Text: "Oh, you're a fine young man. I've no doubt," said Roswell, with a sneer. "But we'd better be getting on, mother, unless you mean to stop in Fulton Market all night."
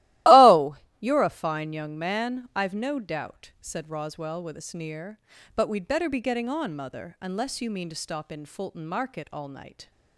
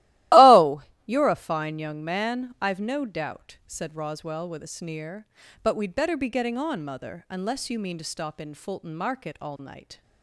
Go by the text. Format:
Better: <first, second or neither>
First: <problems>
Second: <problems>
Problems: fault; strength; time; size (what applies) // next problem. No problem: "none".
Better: neither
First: starts louder than the rest; strong; until 1.5 s; 16.5 dB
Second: starts louder than the rest; strong; until 1.5 s; 16.5 dB